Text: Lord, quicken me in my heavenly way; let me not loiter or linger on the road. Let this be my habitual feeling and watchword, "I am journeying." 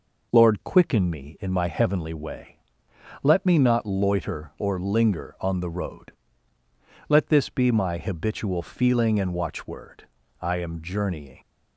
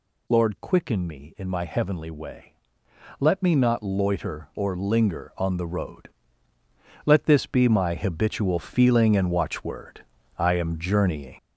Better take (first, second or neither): first